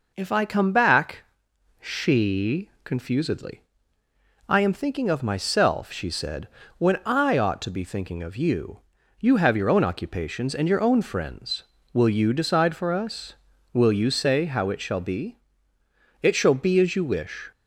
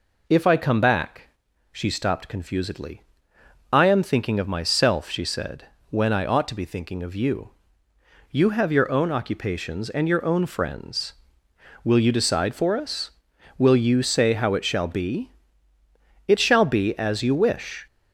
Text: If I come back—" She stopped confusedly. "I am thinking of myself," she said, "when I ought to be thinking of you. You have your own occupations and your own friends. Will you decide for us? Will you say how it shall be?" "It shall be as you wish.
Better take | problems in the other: second | skips "stopped"; at 2.7 s

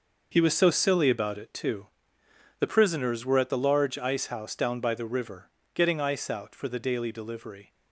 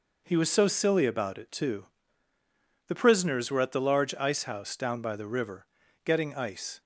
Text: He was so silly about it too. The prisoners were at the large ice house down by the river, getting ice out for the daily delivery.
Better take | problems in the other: first | stops before "out for the daily delivery"; at 6.8 s

